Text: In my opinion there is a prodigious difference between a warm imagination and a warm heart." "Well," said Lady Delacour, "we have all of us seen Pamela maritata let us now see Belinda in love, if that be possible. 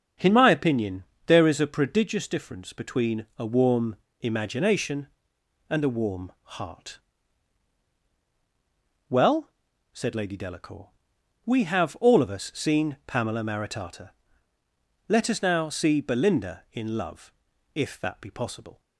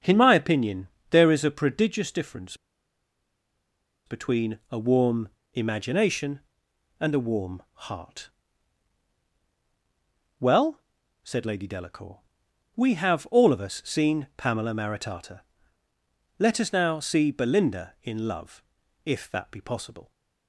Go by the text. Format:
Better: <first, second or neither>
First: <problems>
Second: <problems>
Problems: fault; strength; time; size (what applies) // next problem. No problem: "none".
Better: first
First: starts louder than the rest; until 1.4 s; 7 dB // pauses between "opinion" and "there"; slight; at 1.0 s; 0.22 s long // pauses between "warm" and "imagination"; slight; at 3.9 s; 0.24 s long // pauses between "maritata" and "let"; noticeable; at 14.1 s; 0.98 s long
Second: starts louder than the rest; until 1.2 s; 7 dB // pauses between "opinion" and "there"; slight; at 0.8 s; 0.22 s long // pauses between "difference" and "between"; strong; at 2.5 s; 1.5 s long // pauses between "warm" and "imagination"; slight; at 5.2 s; 0.24 s long // pauses between "maritata" and "let"; noticeable; at 15.4 s; 0.98 s long